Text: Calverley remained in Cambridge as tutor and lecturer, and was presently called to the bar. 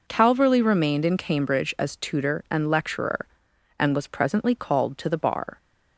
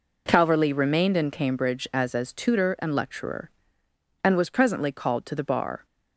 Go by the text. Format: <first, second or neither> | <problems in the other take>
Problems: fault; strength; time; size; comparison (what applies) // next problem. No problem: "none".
first | says "as" twice; at 2.1 s